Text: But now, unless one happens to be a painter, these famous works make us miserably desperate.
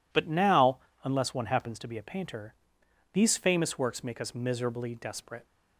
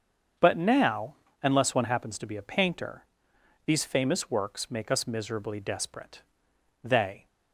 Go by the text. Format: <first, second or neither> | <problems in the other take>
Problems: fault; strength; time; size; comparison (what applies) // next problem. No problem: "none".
first | starts louder than the rest; until 1.6 s; 7 dB // goes on to say "They"; slight; from 6.8 s on; 0.44 s long